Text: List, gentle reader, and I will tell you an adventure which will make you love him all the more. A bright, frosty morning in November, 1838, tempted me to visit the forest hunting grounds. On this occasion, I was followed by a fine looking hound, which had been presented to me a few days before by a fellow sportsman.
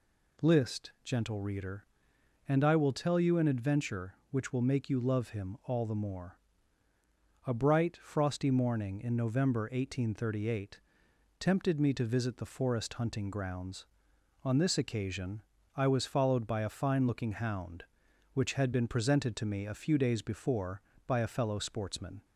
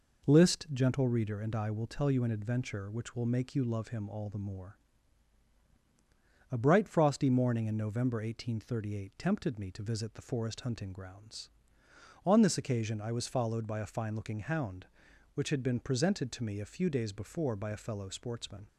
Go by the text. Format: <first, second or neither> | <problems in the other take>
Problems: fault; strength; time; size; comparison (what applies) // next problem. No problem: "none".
neither | none